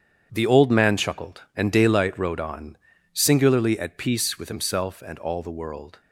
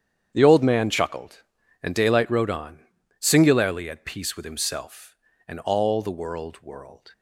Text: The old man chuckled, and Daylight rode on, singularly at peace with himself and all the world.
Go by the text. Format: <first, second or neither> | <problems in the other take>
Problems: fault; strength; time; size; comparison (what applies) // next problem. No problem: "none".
first | starts louder than the rest; strong; until 1.3 s; 8.5 dB; strong in the first // says "world" twice; at 6.6 s